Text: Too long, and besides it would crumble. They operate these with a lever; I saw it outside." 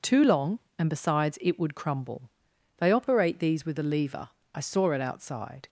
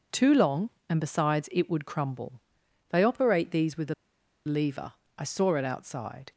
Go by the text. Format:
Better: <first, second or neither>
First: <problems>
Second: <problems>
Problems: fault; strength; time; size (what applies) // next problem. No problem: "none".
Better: first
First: none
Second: pauses between "a" and "lever"; noticeable; at 3.9 s; 0.51 s long